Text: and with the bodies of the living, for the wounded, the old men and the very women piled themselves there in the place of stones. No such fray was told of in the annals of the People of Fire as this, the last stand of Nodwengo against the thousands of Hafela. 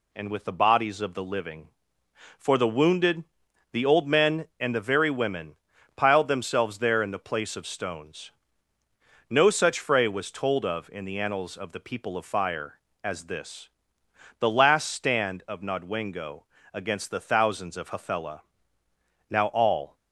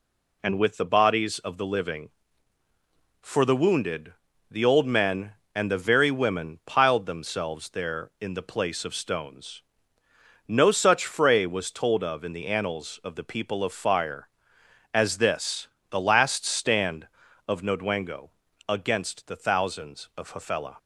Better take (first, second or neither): second